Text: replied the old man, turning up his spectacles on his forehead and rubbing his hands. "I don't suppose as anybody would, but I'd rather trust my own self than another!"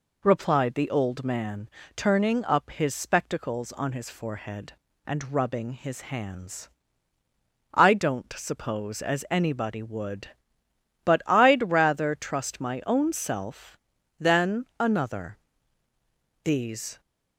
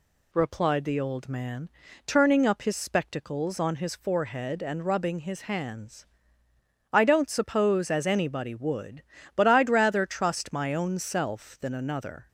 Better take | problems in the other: second | goes on to say "These"; from 16.4 s on; 0.56 s long

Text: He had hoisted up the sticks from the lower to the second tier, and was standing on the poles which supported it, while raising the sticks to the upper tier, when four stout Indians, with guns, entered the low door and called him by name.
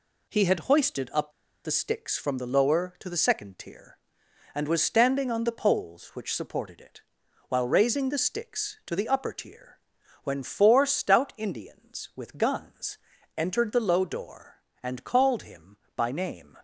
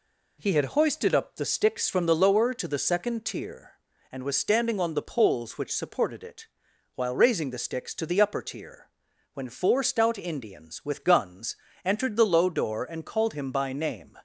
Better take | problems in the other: second | pauses between "up" and "the"; slight; at 1.3 s; 0.32 s long

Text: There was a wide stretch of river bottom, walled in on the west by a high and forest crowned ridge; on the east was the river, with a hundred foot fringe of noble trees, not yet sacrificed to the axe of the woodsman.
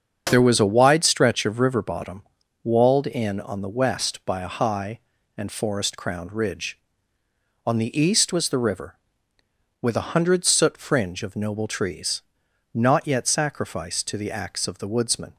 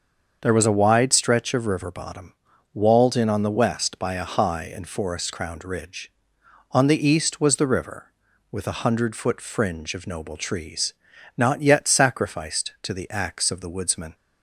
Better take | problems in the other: second | starts louder than the rest; strong; until 1.3 s; 7 dB; also in the second // says "soot" for "foot"; at 10.4 s

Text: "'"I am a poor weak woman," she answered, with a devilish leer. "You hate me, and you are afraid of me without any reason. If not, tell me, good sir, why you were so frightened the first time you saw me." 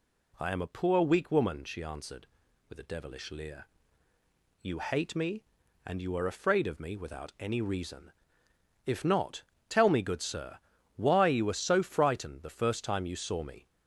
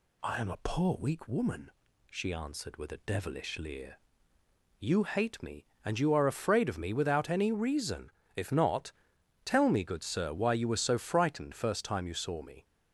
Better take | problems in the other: first | skips "the"; at 11.5 s

